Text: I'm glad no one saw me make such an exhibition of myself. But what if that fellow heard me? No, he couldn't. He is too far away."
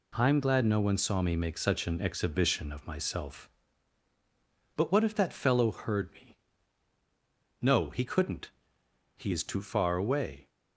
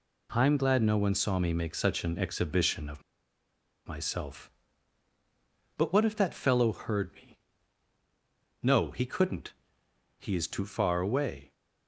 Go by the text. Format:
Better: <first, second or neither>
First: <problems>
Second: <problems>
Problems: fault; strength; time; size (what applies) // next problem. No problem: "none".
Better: first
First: none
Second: pauses between "of" and "myself"; noticeable; at 3.0 s; 0.84 s long